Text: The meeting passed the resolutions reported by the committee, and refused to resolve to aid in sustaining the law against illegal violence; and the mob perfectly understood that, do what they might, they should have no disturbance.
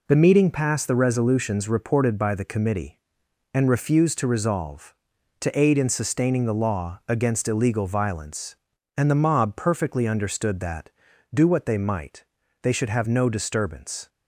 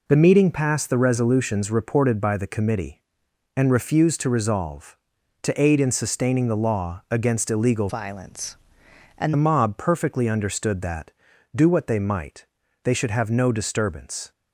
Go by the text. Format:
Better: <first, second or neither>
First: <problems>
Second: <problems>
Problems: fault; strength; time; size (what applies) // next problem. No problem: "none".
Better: first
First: none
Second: changes voice from "violence" to "and"; from 7.8 to 9.3 s; 1.5 s long